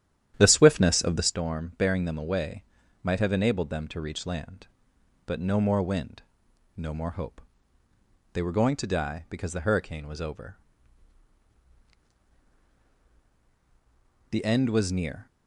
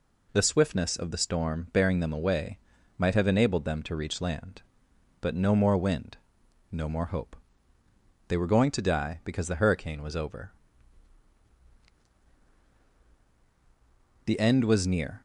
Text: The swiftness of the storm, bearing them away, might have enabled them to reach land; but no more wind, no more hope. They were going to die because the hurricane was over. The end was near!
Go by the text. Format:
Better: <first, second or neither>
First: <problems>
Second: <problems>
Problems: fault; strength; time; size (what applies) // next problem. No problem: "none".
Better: second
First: starts louder than the rest; strong; until 1.4 s; 10.5 dB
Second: none